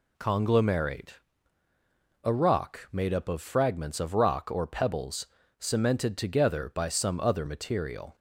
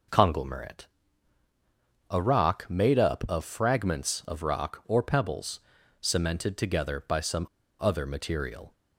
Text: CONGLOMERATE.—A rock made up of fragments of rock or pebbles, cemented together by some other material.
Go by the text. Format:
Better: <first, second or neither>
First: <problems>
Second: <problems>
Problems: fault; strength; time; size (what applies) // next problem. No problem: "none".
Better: first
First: none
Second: pauses between "some" and "other"; slight; at 7.4 s; 0.35 s long